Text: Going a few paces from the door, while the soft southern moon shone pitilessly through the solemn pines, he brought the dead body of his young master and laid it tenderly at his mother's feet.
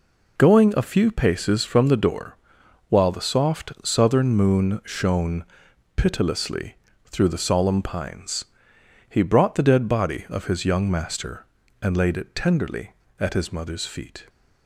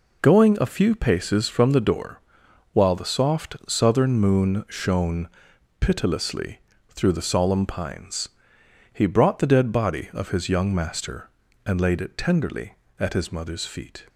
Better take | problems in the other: neither | pauses between "shone" and "pitilessly"; noticeable; the same in both // pauses between "pitilessly" and "through"; slight; the same in both

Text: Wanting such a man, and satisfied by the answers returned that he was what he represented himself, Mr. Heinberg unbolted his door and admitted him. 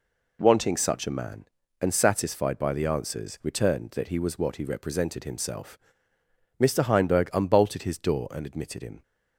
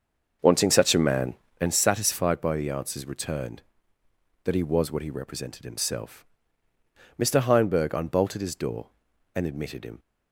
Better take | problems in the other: first | starts louder than the rest; until 1.9 s; 6.5 dB

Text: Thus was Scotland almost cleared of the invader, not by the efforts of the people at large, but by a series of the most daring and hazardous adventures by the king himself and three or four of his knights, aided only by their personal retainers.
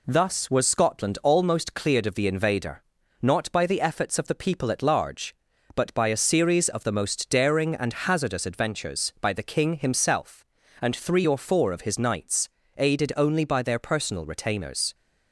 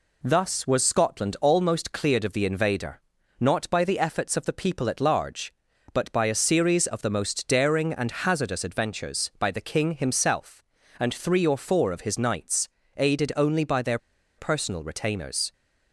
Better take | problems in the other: first | pauses between "their" and "personal"; at 13.9 s; 0.40 s long

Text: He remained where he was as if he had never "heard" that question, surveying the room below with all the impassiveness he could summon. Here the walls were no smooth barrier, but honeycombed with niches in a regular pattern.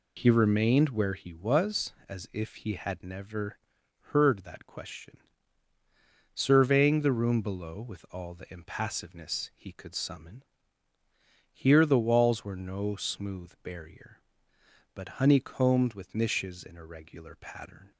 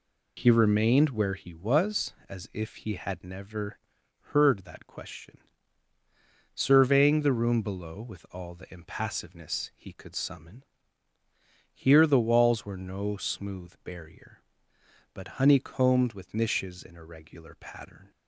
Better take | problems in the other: neither | pauses between "never" and "heard"; noticeable; the same in both

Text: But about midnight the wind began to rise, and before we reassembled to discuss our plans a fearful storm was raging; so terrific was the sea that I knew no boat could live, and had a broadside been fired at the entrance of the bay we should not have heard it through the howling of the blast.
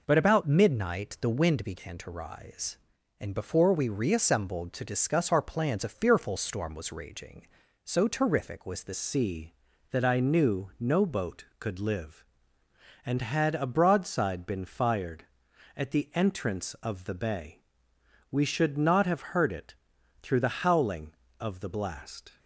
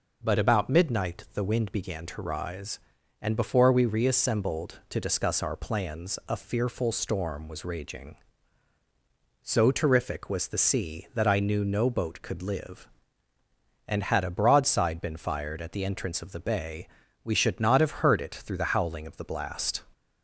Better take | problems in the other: second | changes voice at "sea"; from 8.9 s on; 13.4 s long // pauses between "bay" and "we"; noticeable; at 17.5 s; 0.72 s long; also in the second // pauses between "it" and "through"; noticeable; at 19.7 s; 0.48 s long

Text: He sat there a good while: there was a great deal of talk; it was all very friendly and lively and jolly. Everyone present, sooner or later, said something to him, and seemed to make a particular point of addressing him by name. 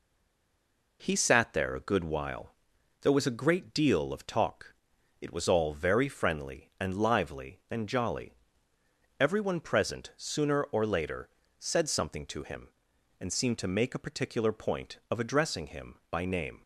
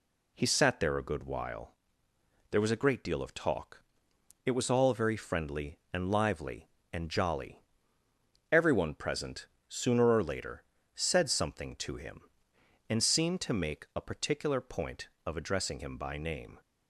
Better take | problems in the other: second | stays silent before the first word; until 0.9 s; 0.9 s long

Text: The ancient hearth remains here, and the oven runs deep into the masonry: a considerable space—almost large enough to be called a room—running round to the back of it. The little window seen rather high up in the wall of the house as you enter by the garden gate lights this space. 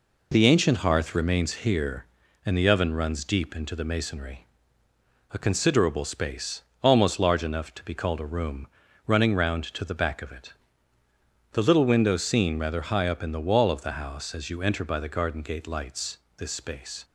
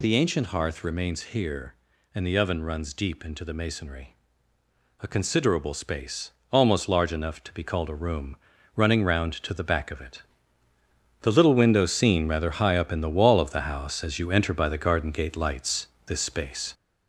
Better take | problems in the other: first | gets louder; noticeable; throughout; 5.5 dB // pauses between "lights" and "this"; slight; at 15.8 s; 0.22 s long; slight in the first

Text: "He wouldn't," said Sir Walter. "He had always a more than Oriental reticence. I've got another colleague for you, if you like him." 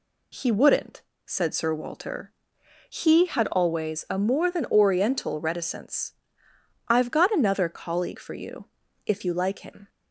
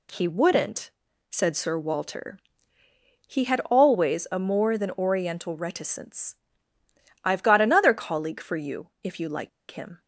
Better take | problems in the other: first | pauses between "like" and "him"; slight; at 9.4 s; 0.21 s long

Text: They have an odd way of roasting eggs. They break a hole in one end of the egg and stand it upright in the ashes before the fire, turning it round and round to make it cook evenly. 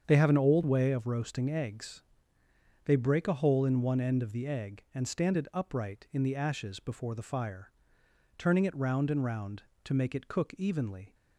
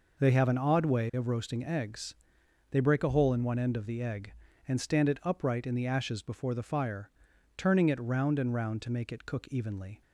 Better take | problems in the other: second | starts louder than the rest; strong; until 1.1 s; 7.5 dB // says "old" for "odd"; at 0.3 s

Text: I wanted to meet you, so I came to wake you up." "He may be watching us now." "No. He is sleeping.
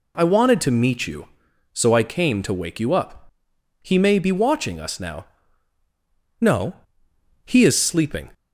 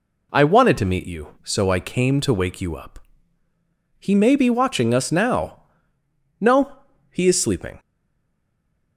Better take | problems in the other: first | stays silent after the last word; from 7.7 s on; 1.2 s long

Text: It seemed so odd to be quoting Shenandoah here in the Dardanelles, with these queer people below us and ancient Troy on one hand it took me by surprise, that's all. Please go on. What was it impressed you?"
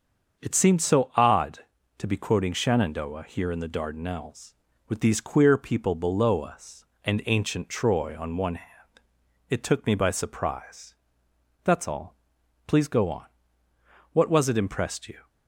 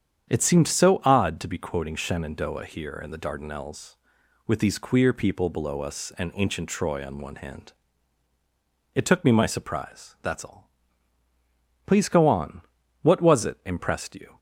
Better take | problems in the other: first | starts louder than the rest; strong; until 1.3 s; 8 dB; also in the first // pauses between "hand" and "it"; at 7.7 s; 1.2 s long; noticeable in the first // says "my" for "by"; at 9.2 s

